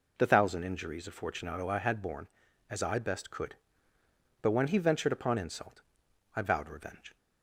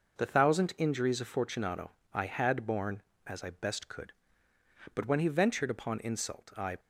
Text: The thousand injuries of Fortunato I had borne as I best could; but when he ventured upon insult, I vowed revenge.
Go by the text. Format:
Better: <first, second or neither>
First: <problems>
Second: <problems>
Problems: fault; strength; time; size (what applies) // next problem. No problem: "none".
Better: first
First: none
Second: pauses between "Fortunato" and "I"; slight; at 1.9 s; 0.20 s long // stops before "vowed revenge"; at 6.7 s